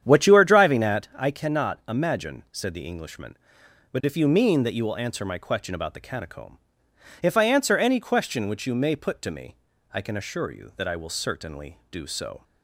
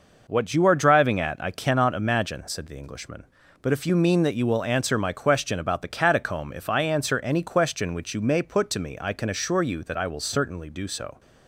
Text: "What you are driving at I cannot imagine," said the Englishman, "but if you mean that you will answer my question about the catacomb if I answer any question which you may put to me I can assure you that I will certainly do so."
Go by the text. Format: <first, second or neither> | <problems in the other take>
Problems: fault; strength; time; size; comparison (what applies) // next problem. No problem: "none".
second | starts louder than the rest; strong; until 1.1 s; 9 dB // pauses between "catacomb" and "if"; noticeable; at 6.5 s; 0.64 s long // pauses between "me" and "I"; at 9.5 s; 0.40 s long